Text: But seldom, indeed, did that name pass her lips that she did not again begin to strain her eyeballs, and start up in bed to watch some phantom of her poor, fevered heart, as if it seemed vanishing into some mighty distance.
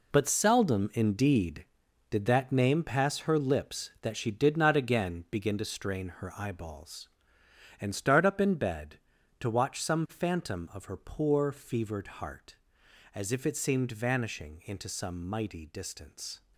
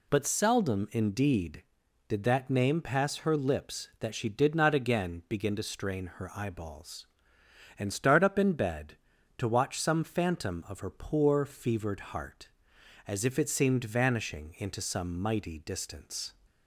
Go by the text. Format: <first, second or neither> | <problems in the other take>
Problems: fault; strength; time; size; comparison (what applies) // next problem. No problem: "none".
second | gets quieter; strong; throughout; 10.5 dB